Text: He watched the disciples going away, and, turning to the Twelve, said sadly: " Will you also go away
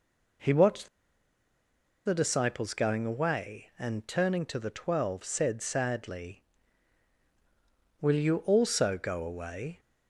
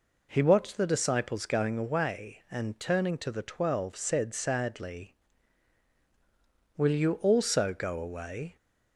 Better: second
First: pauses between "watched" and "the"; at 0.8 s; 1.1 s long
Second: none

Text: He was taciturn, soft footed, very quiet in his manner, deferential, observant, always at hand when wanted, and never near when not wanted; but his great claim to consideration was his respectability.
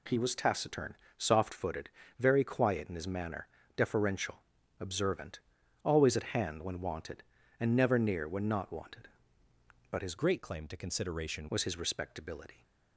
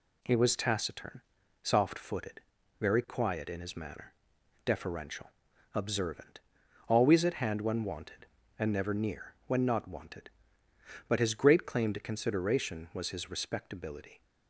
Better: second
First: changes voice from "great" to "consideration"; from 10.1 to 11.4 s; 1.3 s long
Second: none

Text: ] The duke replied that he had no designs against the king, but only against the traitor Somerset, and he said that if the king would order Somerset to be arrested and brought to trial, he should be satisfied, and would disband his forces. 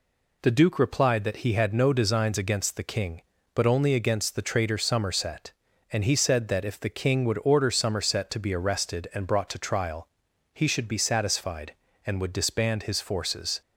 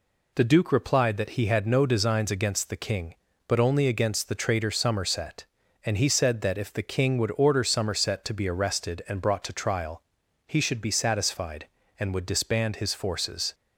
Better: neither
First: none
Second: none

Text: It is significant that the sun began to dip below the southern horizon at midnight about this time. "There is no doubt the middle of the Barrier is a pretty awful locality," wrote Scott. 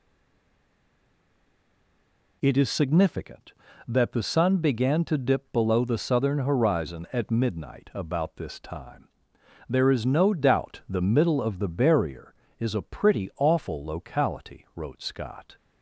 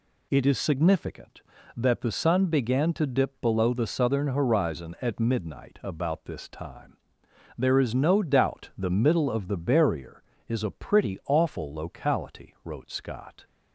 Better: second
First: stays silent before the first word; until 2.4 s; 2.4 s long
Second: none

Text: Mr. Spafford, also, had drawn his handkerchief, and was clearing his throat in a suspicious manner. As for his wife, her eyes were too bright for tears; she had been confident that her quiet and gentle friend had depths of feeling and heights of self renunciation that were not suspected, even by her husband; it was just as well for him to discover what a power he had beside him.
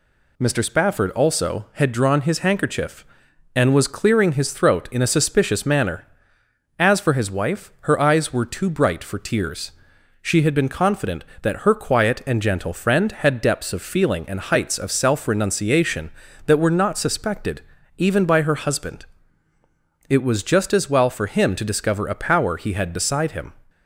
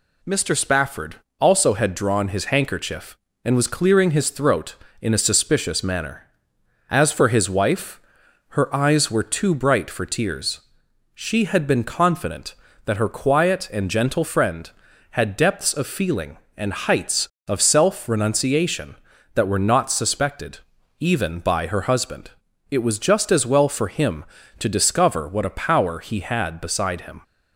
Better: second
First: skips "what"; at 22.0 s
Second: none

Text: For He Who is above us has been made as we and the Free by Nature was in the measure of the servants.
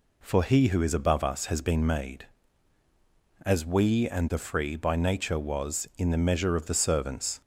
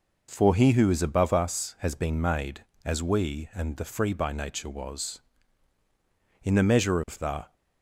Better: first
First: none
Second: stops before "servants"; at 7.5 s

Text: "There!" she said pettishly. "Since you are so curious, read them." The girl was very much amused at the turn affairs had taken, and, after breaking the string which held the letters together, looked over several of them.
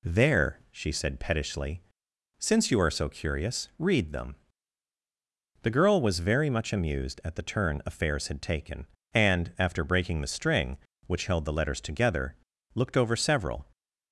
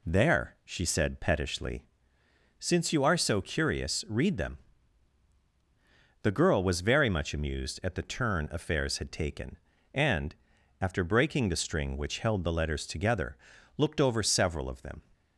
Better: second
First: stops before "of them"; at 13.7 s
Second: none

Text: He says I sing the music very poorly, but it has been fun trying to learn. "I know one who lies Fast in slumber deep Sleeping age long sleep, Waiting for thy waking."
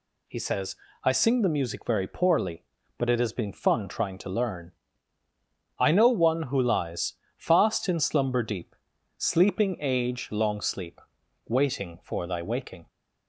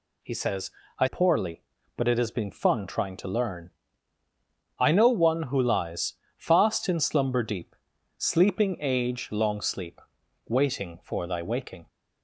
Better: first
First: pauses between "says" and "I"; slight; at 0.7 s; 0.30 s long // pauses between "lies" and "Fast"; slight; at 7.1 s; 0.24 s long // pauses between "deep" and "Sleeping"; at 8.7 s; 0.44 s long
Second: pauses between "says" and "I"; slight; at 0.6 s; 0.30 s long // skips "sing the music very"; at 1.0 s // pauses between "lies" and "Fast"; slight; at 6.1 s; 0.24 s long // pauses between "deep" and "Sleeping"; at 7.7 s; 0.44 s long

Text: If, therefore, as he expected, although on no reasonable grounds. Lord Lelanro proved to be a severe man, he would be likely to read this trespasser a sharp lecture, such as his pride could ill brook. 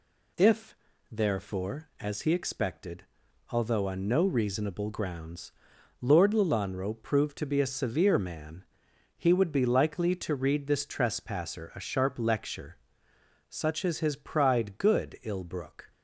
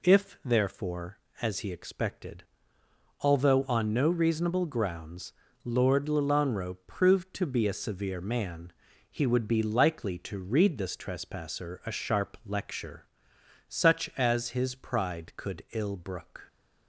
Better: second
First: says "good" for "could"; at 14.7 s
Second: none

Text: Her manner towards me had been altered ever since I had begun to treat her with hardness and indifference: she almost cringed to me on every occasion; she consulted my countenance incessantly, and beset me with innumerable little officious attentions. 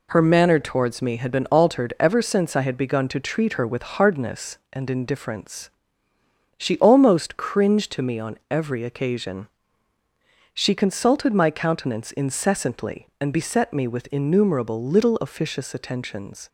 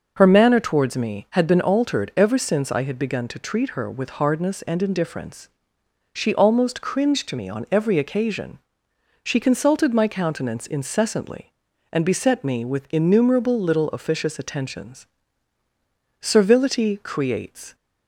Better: first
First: none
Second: goes on to say "Servility creates"; from 16.1 s on; 1.5 s long

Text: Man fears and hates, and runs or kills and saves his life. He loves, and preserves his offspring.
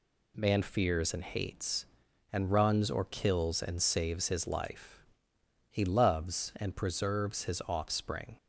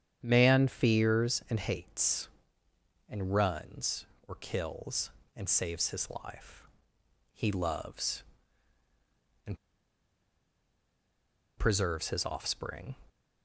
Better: first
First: none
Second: starts louder than the rest; strong; until 1.2 s; 9 dB // pauses between "and" and "preserves"; strong; at 9.5 s; 2.0 s long

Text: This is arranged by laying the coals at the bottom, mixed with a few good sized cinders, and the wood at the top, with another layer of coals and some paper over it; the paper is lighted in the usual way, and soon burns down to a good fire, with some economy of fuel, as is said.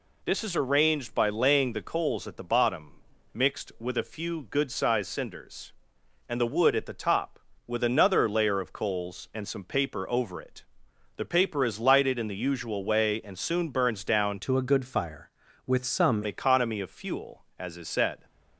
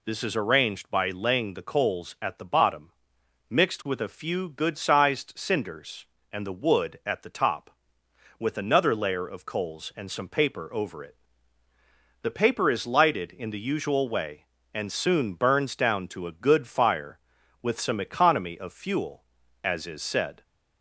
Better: second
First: changes voice from "to" to "some"; from 14.3 to 16.2 s; 1.9 s long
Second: none

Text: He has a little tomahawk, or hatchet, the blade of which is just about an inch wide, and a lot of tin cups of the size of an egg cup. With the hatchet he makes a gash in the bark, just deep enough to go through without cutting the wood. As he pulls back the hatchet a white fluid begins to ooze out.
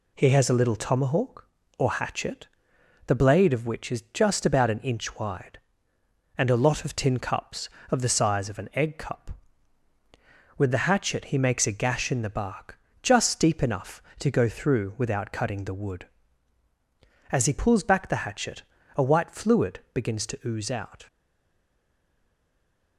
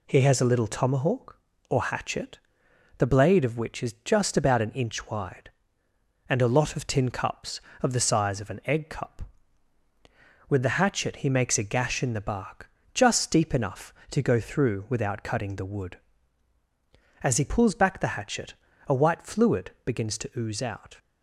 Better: second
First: pauses between "hatchet" and "a"; slight; at 18.6 s; 0.32 s long // stays silent after the last word; noticeable; from 21.0 s on; 1.9 s long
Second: pauses between "hatchet" and "a"; slight; at 18.5 s; 0.32 s long

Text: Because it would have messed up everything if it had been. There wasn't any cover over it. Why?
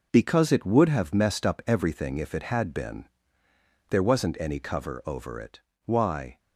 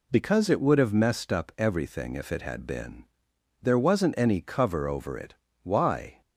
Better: second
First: gets quieter; strong; throughout; 7.5 dB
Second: none

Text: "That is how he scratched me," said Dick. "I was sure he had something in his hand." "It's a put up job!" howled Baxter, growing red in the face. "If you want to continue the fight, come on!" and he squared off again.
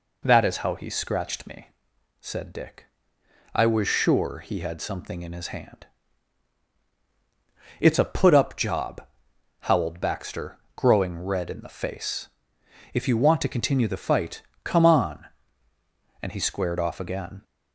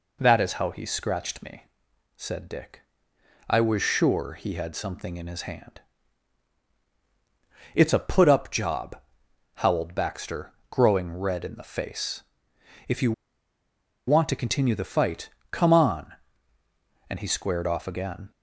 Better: first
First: none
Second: pauses between "you" and "want"; noticeable; at 13.1 s; 0.93 s long

